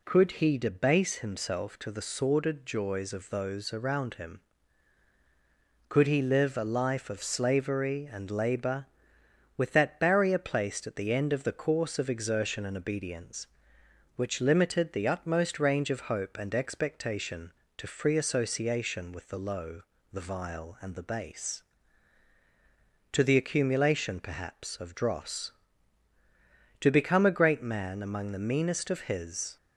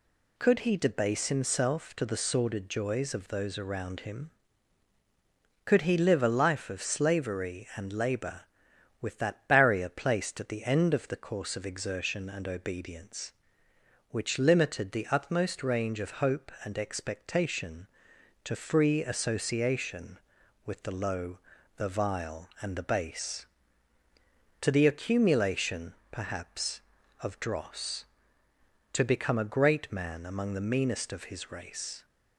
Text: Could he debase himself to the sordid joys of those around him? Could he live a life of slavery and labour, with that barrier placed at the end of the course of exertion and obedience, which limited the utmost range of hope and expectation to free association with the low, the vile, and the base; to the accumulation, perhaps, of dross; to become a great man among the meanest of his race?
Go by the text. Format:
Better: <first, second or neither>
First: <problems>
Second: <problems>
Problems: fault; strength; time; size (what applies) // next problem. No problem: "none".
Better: second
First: stops before "race"; at 29.5 s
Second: none